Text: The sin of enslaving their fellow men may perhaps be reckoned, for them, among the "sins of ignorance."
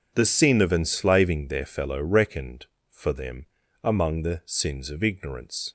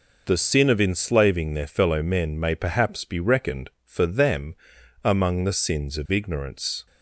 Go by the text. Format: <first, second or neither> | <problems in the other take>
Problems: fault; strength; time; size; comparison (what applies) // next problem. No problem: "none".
second | skips "men may perhaps be"; at 2.0 s